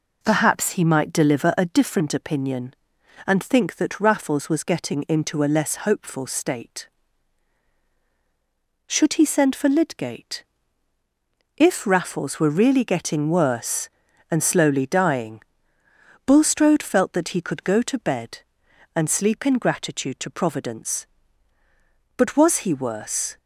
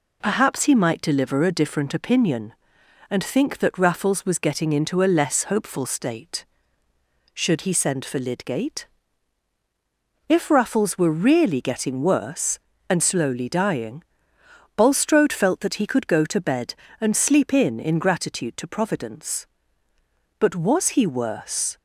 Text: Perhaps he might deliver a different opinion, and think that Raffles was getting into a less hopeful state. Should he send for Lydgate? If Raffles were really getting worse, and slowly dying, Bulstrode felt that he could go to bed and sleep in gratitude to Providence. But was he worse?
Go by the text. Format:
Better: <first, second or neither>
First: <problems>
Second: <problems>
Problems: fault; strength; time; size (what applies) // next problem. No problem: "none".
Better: first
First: none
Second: says "in" twice; at 17.7 s